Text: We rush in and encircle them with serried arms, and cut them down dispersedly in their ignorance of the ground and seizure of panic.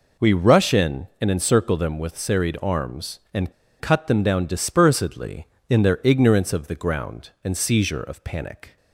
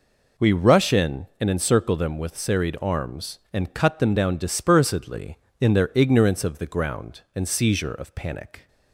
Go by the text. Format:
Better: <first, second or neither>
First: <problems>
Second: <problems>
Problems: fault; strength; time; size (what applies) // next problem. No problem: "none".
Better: second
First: pauses between "and" and "cut"; slight; at 3.5 s; 0.27 s long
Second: none